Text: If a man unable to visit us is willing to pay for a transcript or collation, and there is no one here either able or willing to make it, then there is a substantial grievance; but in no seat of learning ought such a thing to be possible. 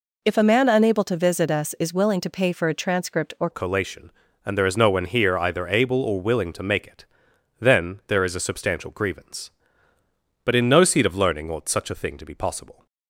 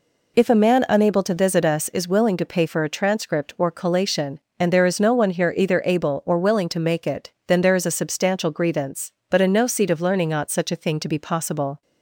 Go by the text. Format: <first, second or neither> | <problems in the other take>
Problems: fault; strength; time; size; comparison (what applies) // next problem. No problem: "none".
second | changes voice at "collation"; from 3.5 s on; 9.3 s long